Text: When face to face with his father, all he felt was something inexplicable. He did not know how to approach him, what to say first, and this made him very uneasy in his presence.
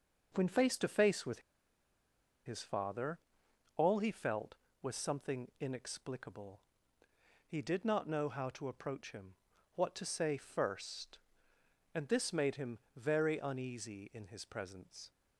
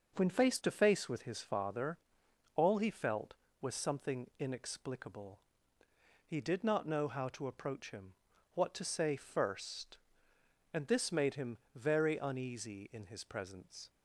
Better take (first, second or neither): second